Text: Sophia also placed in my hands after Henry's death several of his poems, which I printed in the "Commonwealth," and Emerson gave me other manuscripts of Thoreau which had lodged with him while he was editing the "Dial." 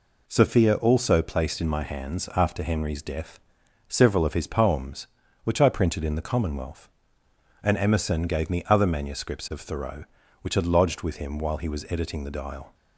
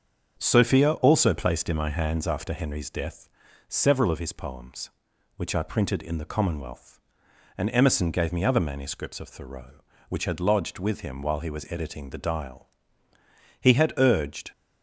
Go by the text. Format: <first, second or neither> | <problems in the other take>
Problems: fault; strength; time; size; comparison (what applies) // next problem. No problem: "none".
first | starts louder than the rest; until 1.4 s; 7 dB // pauses between "death" and "several"; at 3.2 s; 0.42 s long; noticeable in the first // goes on to say "He had urged"; noticeable; from 13.6 s on; 0.90 s long